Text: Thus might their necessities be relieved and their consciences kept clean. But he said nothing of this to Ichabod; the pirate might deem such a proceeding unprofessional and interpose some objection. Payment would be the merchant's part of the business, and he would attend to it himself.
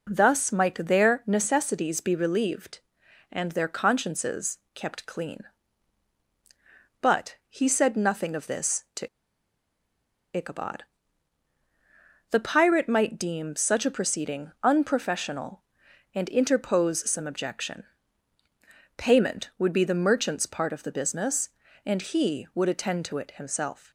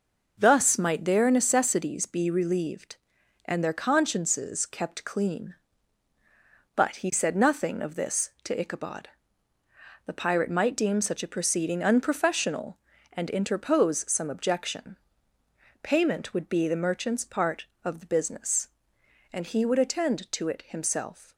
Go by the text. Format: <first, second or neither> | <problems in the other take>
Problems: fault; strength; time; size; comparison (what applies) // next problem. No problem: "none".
second | pauses between "consciences" and "kept"; slight; at 4.5 s; 0.16 s long // pauses between "to" and "Ichabod"; strong; at 9.0 s; 1.2 s long